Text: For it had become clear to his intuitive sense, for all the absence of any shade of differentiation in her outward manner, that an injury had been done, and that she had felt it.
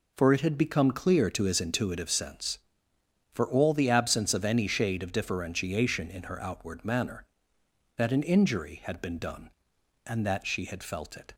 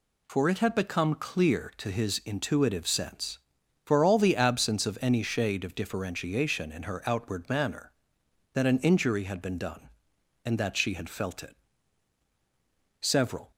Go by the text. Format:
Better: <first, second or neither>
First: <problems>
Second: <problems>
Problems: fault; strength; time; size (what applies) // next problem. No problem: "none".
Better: first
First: none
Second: goes on to say "Several"; from 13.0 s on; 0.50 s long